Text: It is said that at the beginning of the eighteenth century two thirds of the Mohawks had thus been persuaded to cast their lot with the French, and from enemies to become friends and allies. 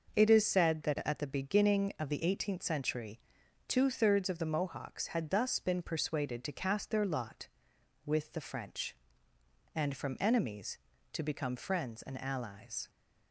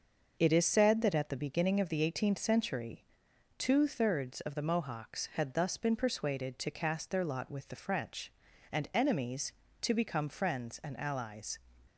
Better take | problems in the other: first | starts louder than the rest; noticeable; until 1.4 s; 6 dB // pauses between "century" and "two"; noticeable; at 3.0 s; 0.56 s long; noticeable in the first // skips "from"; at 8.9 s

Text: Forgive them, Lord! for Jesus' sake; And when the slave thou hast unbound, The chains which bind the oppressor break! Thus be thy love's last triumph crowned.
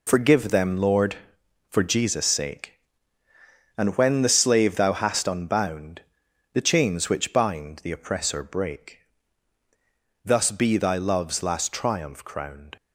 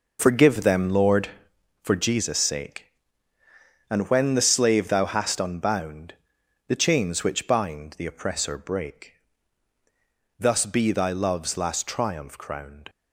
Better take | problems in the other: first | starts louder than the rest; noticeable; until 1.8 s; 5 dB

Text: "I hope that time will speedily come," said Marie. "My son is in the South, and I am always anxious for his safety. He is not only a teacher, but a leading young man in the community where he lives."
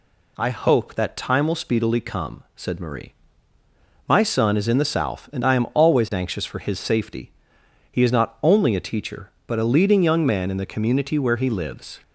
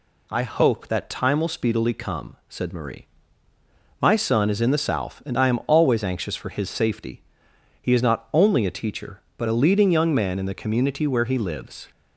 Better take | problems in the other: neither | none

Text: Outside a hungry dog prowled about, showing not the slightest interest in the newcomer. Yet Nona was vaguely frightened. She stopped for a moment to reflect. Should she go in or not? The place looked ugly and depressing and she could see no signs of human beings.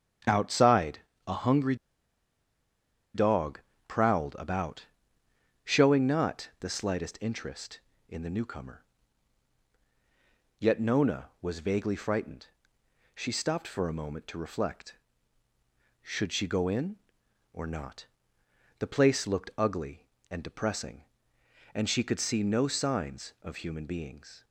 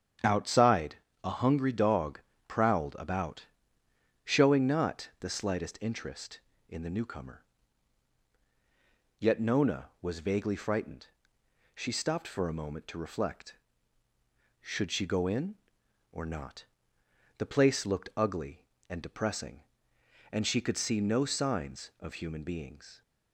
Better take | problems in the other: second | starts louder than the rest; strong; until 1.5 s; 8.5 dB; strong in the second // pauses between "Outside" and "a"; slight; at 0.9 s; 0.28 s long; slight in the second // pauses between "hungry" and "dog"; strong; at 1.7 s; 1.3 s long // pauses between "dog" and "prowled"; slight; at 3.5 s; 0.26 s long; slight in the second

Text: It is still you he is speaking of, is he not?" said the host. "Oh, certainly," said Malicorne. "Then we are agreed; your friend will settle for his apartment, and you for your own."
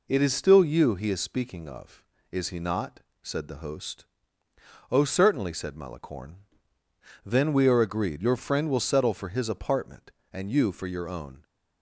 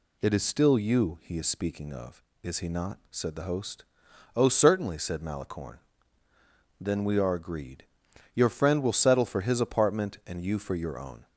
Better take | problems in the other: neither | none

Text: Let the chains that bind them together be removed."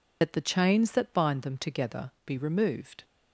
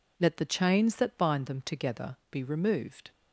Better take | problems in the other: second | loses the start of "Let"; at 0.2 s; 75 ms // pauses between "together" and "be"; slight; at 2.0 s; 0.16 s long; slight in the second

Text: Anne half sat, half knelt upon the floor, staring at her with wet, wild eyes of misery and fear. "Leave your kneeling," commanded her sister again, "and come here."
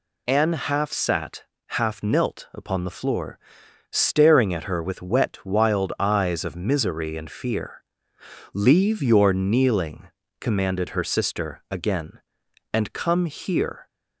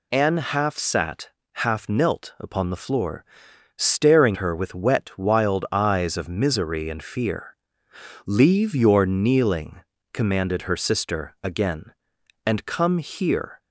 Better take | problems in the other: first | skips "at"; at 4.3 s

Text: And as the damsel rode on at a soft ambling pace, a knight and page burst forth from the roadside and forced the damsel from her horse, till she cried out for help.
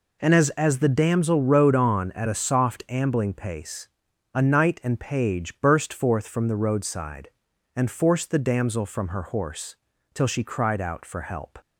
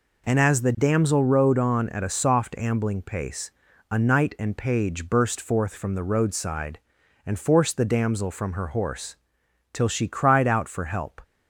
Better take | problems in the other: second | says "as" twice; at 0.5 s

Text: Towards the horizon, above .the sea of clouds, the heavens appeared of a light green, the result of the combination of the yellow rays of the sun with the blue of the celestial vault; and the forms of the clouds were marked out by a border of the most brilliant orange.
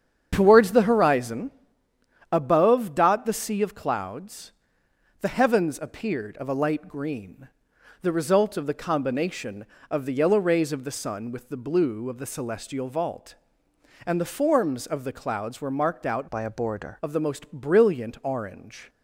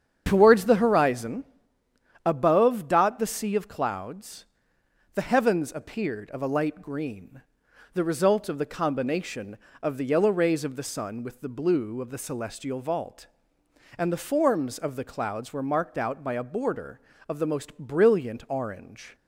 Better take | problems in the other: second | starts louder than the rest; strong; until 1.3 s; 8 dB; strong in the second // changes voice from "by" to "border"; from 16.2 to 16.9 s; 0.7 s long

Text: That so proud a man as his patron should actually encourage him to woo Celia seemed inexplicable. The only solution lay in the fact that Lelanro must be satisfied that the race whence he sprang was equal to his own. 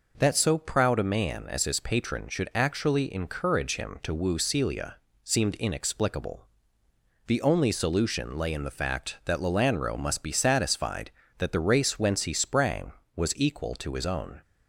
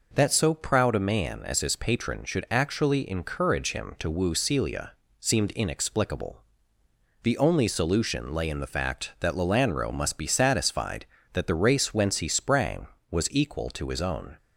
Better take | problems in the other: neither | pauses between "Celia" and "seemed"; slight; the same in both

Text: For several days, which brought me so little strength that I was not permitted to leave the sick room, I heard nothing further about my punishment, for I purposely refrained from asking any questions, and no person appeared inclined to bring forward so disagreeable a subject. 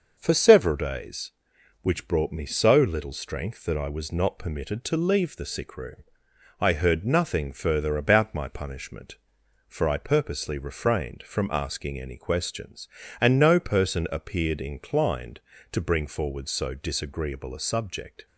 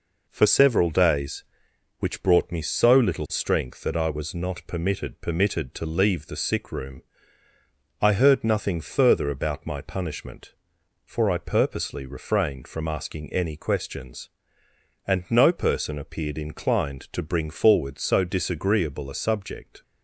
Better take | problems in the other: first | says "permitted" twice; at 5.2 s

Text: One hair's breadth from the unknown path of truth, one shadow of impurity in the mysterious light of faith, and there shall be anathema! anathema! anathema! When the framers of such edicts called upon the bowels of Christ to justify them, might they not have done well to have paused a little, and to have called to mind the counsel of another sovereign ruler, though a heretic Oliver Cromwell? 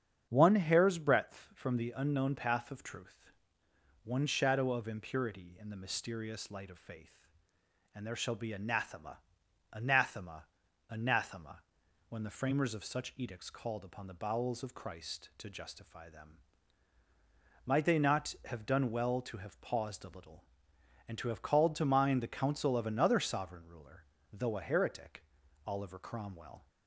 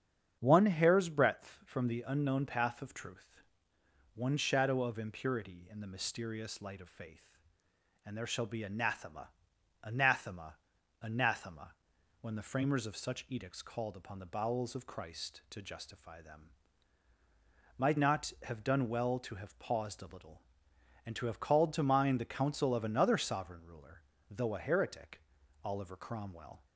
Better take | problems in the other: first | starts louder than the rest; strong; until 1.4 s; 8 dB; strong in the first // skips "they"; at 17.9 s // pauses between "heretic" and "Oliver"; at 25.2 s; 0.42 s long; also in the first

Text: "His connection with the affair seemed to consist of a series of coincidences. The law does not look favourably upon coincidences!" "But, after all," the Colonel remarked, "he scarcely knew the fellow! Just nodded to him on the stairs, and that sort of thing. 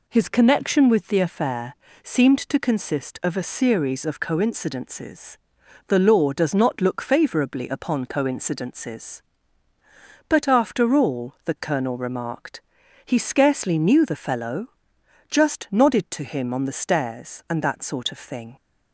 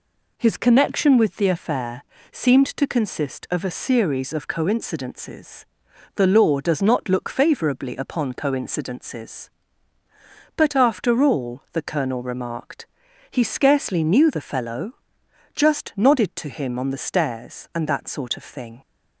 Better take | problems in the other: neither | pauses between "affair" and "seemed"; slight; the same in both

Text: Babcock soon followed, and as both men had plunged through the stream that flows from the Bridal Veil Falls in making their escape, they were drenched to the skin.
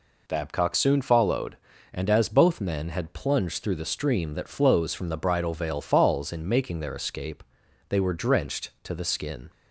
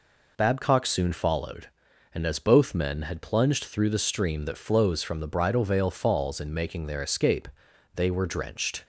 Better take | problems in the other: first | stops before "to the skin"; at 8.8 s

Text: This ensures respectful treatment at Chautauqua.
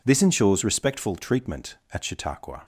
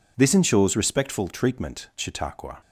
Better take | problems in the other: first | skips "at"; at 1.9 s

